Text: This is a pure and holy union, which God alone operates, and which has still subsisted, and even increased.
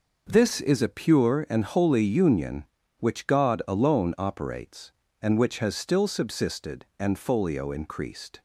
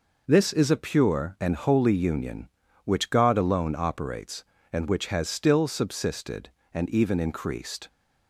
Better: second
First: says "folio" for "even"; at 7.1 s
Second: none

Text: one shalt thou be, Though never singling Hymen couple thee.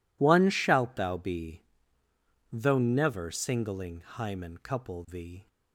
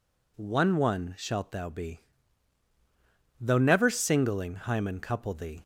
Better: first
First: none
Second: says "one" twice; at 0.7 s

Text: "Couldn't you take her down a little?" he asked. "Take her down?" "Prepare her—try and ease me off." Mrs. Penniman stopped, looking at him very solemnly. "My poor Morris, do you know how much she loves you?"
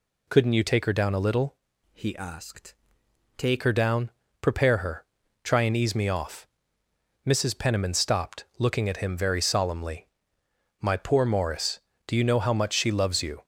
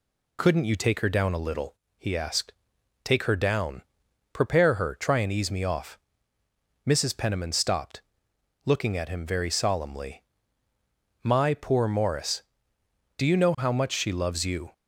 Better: second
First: changes voice from "he" to "Take"; from 1.9 to 3.6 s; 1.7 s long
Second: none

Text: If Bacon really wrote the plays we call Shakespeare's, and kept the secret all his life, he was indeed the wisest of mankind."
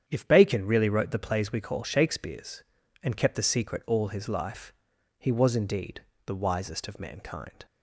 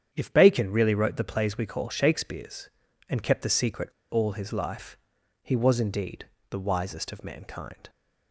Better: first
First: starts louder than the rest; strong; until 1.0 s; 8.5 dB // pauses between "indeed" and "the"; slight; at 6.0 s; 0.26 s long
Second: starts louder than the rest; strong; until 1.1 s; 8.5 dB // pauses between "secret" and "all"; slight; at 3.8 s; 0.23 s long // pauses between "indeed" and "the"; slight; at 6.2 s; 0.26 s long

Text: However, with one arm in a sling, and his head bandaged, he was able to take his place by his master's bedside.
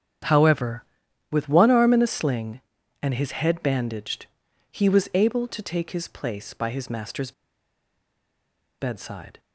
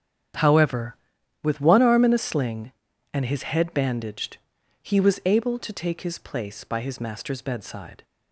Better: second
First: starts louder than the rest; strong; until 1.7 s; 9 dB // pauses between "master's" and "bedside"; strong; at 7.3 s; 1.4 s long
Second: starts louder than the rest; strong; until 1.8 s; 9 dB

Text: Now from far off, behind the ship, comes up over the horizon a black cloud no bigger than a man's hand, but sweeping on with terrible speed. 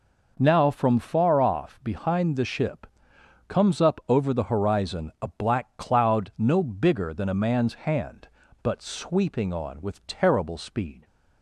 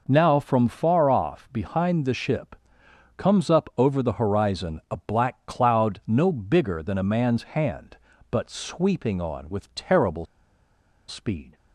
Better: first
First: none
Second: pauses between "terrible" and "speed"; noticeable; at 10.2 s; 0.82 s long

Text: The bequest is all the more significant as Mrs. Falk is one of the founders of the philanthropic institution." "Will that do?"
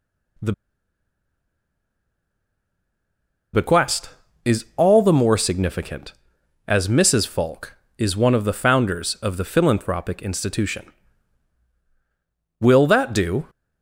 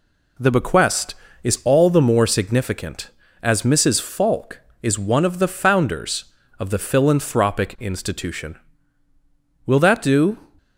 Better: second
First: pauses between "The" and "bequest"; strong; at 0.5 s; 3.0 s long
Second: none

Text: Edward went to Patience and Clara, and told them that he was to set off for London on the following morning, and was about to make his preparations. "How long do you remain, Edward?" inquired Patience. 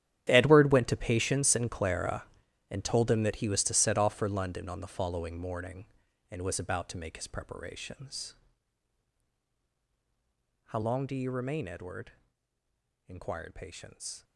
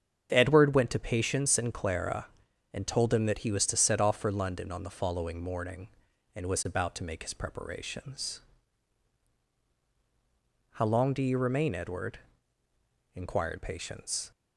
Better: second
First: gets quieter; strong; throughout; 15 dB // starts louder than the rest; strong; until 1.2 s; 11 dB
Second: starts louder than the rest; strong; until 1.3 s; 7.5 dB

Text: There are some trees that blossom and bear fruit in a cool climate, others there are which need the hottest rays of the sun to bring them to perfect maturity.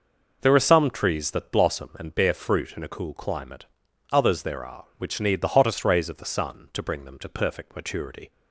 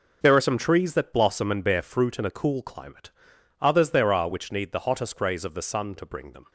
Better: first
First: none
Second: stops before "to perfect maturity"; at 6.4 s

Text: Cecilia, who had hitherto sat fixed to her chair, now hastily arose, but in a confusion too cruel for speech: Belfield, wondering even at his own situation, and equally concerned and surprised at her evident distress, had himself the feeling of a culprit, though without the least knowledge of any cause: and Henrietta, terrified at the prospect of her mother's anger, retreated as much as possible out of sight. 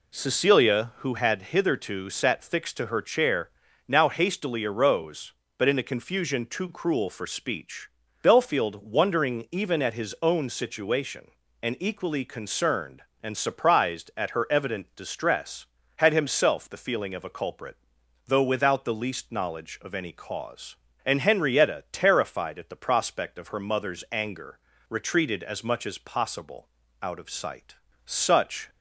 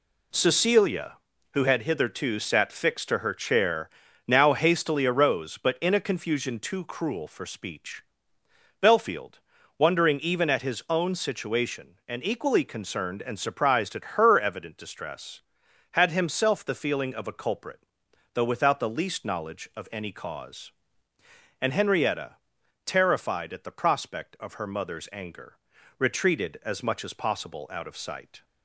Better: second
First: pauses between "possible" and "out"; slight; at 26.6 s; 0.32 s long // goes on to say "Such"; noticeable; from 28.0 s on; 0.64 s long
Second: none

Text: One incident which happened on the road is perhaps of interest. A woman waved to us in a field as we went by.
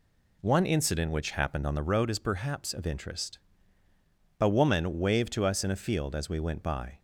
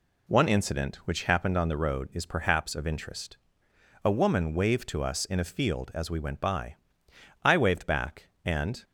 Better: first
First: none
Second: goes on to say "I waved back and"; from 7.4 s on; 1.4 s long

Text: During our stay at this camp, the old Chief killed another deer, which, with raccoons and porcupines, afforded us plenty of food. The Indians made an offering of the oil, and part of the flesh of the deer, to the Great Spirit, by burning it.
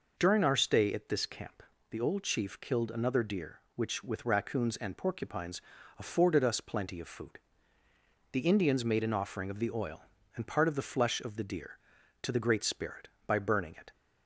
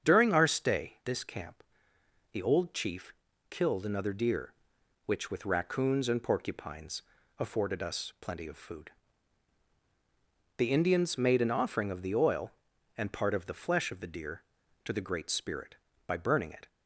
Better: first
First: none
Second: starts louder than the rest; strong; until 1.1 s; 7.5 dB // skips "at"; at 1.0 s // pauses between "Chief" and "killed"; slight; at 3.1 s; 0.36 s long

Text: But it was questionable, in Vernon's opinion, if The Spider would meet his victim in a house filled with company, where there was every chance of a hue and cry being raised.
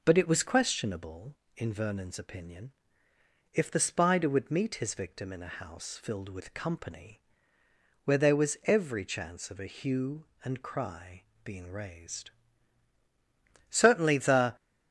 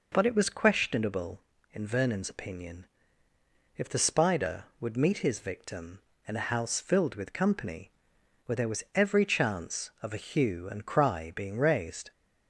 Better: second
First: pauses between "cry" and "being"; slight; at 11.2 s; 0.20 s long // goes on to say "Certainly the"; noticeable; from 13.6 s on; 0.86 s long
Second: none

